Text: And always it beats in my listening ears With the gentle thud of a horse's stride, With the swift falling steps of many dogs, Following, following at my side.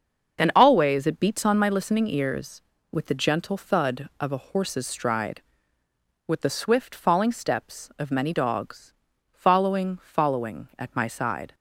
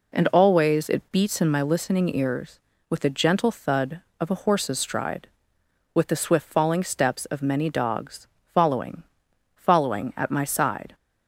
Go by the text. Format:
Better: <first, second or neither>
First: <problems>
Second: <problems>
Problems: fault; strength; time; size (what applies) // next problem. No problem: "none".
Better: second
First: starts louder than the rest; until 1.4 s; 6.5 dB // says "on" for "in"; at 1.4 s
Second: none